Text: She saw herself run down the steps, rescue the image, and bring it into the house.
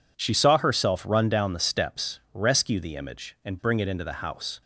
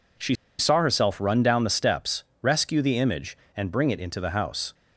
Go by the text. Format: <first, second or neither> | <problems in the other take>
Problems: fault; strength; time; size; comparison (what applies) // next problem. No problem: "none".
first | pauses between "She" and "saw"; slight; at 0.3 s; 0.24 s long